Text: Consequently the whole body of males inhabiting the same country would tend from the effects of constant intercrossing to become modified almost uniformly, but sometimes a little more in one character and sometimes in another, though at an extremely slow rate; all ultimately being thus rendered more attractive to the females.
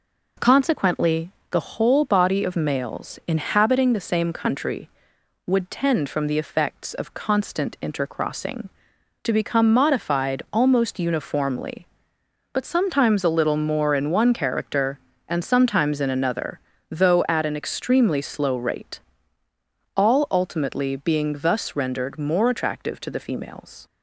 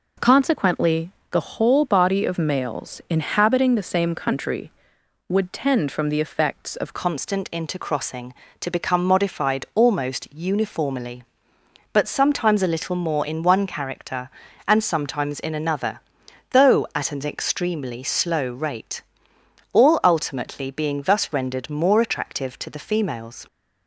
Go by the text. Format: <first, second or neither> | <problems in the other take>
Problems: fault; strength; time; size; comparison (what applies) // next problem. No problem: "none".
first | pauses between "Consequently" and "the"; slight; at 1.1 s; 0.20 s long; slight in the first // changes voice at "constant"; from 6.9 s on; 16.5 s long